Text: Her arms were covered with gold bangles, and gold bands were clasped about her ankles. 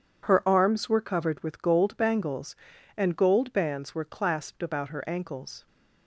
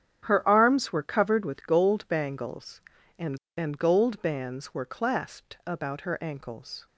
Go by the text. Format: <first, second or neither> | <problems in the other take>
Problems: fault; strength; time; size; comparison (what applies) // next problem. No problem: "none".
first | starts louder than the rest; strong; until 1.2 s; 8.5 dB // says "and" twice; at 3.5 s